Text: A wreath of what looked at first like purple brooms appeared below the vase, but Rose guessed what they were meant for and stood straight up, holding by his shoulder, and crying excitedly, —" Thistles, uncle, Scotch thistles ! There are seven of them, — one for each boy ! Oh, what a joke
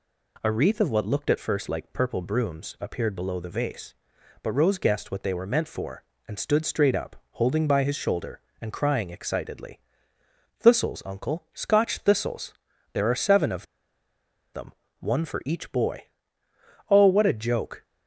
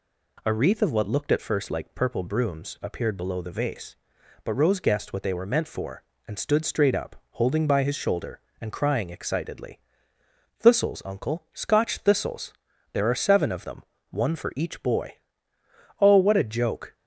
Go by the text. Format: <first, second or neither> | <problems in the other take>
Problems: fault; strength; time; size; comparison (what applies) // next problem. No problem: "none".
second | pauses between "of" and "them"; noticeable; at 13.6 s; 0.88 s long